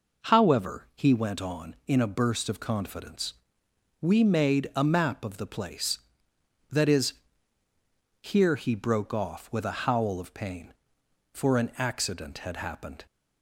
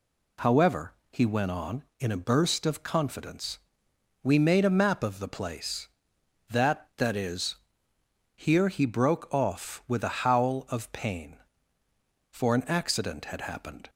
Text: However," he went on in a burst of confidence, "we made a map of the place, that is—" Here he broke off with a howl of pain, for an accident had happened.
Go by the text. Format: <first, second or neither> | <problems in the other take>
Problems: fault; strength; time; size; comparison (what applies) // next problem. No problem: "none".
first | says "that" twice; at 6.9 s